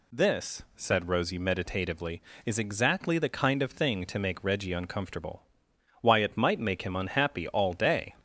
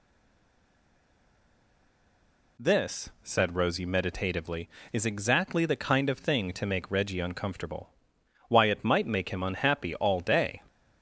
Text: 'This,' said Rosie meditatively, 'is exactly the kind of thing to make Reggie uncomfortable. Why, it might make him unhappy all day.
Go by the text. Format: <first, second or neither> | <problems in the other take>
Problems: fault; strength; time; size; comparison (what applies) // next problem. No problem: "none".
first | stays silent before the first word; strong; until 2.5 s; 2.5 s long